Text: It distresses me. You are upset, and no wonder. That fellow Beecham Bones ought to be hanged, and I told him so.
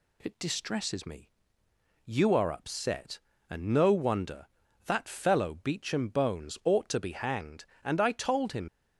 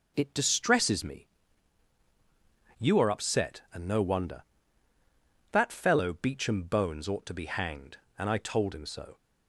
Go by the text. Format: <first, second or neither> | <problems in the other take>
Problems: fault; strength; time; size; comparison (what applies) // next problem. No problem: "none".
second | stops before "so"; at 8.6 s